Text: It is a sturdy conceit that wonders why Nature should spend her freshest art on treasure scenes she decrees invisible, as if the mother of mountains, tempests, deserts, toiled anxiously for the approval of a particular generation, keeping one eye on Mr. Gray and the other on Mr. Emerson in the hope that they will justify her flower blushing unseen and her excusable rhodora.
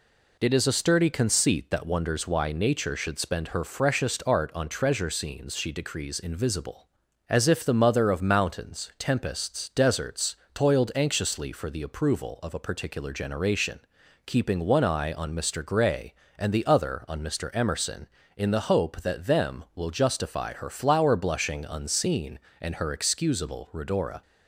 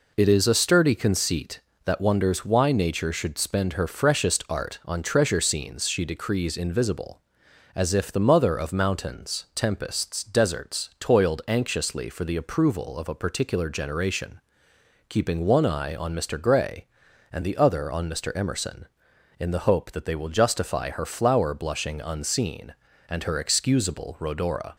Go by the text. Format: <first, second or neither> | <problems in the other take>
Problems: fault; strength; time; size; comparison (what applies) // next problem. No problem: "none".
second | says "them" for "they"; at 19.2 s